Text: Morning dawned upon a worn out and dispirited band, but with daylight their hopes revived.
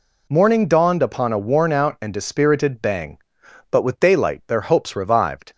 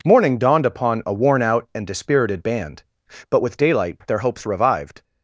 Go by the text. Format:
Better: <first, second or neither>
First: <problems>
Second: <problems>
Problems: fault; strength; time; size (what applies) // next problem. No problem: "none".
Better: second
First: says "bang" for "band"; at 2.7 s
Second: none